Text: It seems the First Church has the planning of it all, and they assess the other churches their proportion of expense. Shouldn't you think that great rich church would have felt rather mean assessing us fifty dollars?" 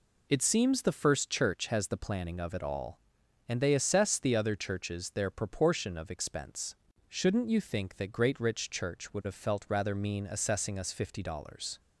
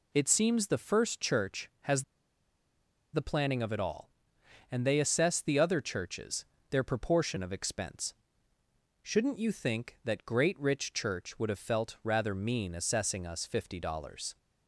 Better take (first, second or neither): first